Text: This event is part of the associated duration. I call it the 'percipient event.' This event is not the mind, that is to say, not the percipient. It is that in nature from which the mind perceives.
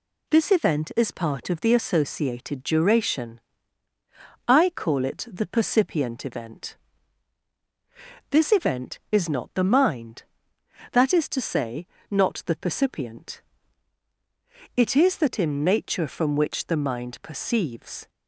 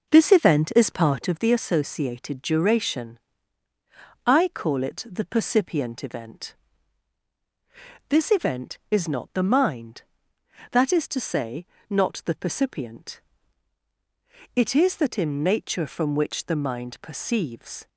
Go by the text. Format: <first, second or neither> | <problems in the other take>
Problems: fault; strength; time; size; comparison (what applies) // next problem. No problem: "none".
first | starts louder than the rest; noticeable; until 1.4 s; 5.5 dB